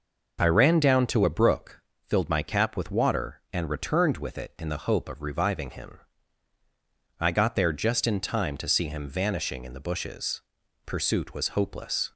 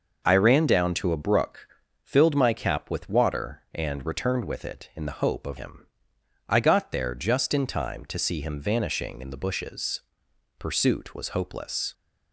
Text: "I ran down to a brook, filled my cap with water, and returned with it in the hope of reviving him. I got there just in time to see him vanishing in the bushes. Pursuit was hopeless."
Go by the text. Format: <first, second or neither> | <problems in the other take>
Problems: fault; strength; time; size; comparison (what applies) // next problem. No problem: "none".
first | skips "reviving"; at 5.5 s